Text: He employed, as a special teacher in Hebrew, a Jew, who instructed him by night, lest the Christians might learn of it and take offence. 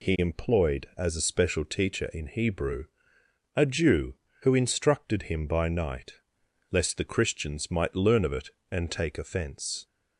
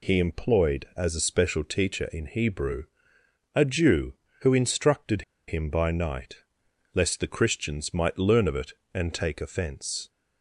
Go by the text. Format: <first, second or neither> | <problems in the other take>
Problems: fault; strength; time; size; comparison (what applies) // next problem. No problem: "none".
first | pauses between "instructed" and "him"; slight; at 5.2 s; 0.26 s long